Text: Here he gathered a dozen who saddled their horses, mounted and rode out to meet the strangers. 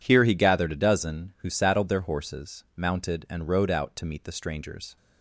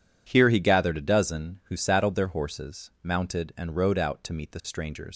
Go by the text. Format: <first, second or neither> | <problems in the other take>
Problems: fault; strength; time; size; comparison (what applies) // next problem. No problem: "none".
first | leaves "strangers" unfinished; at 5.1 s; 125 ms